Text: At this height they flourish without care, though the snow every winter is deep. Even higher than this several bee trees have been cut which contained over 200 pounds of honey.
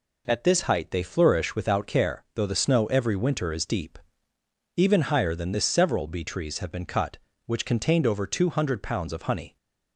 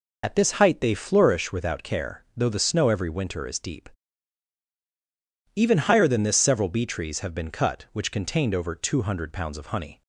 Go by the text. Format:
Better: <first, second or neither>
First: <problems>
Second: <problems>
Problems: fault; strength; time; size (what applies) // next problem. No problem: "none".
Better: first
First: none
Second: loses the start of "At"; at 0.2 s; 50 ms